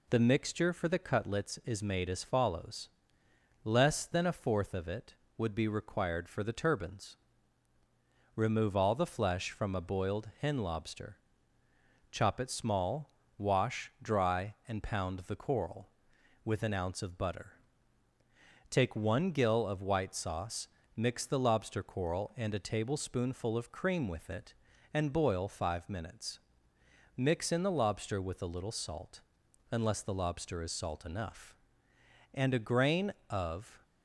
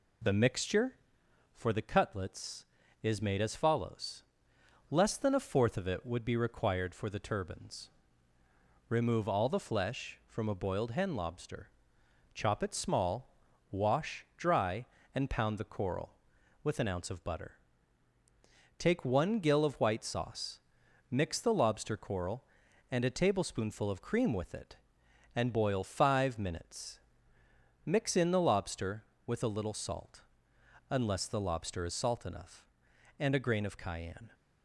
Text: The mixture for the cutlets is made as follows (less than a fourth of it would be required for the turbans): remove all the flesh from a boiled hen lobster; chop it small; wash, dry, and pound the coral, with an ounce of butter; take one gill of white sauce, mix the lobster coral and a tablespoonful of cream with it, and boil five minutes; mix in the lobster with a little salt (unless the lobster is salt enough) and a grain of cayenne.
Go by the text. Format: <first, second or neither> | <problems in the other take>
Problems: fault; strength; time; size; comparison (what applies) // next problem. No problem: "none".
second | stops before "cayenne"; at 33.8 s